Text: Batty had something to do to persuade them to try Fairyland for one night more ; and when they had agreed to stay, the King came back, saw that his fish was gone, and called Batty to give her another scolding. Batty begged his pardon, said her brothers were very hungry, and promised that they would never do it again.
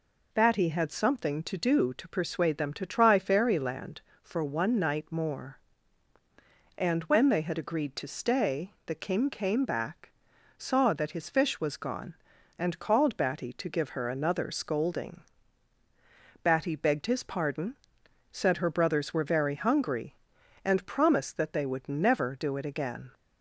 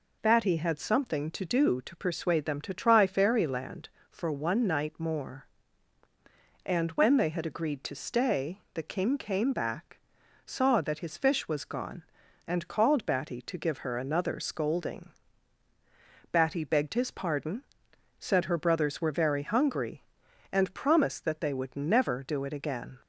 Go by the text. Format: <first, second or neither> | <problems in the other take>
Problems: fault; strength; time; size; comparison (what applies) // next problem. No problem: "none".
neither | none